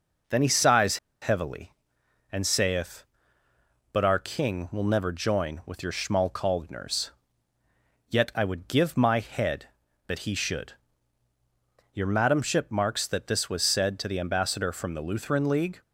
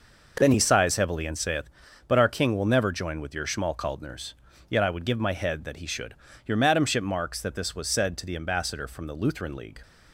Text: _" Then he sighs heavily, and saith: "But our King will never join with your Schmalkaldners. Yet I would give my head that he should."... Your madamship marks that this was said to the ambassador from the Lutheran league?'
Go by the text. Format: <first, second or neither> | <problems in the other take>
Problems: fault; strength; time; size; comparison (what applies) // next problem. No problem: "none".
second | pauses between "sighs" and "heavily"; slight; at 0.9 s; 0.24 s long